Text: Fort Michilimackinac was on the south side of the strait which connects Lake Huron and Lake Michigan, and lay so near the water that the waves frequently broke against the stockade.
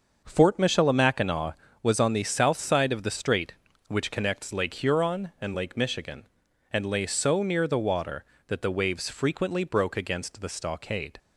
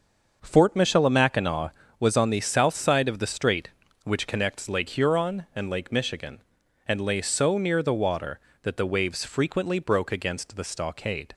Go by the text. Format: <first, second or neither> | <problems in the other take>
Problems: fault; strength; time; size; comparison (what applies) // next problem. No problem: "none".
neither | starts louder than the rest; the same in both